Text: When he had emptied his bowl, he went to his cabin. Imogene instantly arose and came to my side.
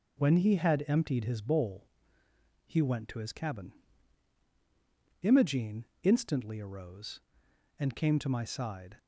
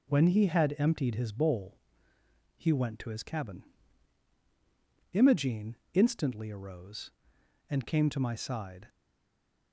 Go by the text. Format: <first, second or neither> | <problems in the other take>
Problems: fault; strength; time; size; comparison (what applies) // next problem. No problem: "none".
first | pauses between "Imogene" and "instantly"; slight; at 5.7 s; 0.16 s long; slight in the first // stays silent after the last word; slight; from 8.8 s on; 0.9 s long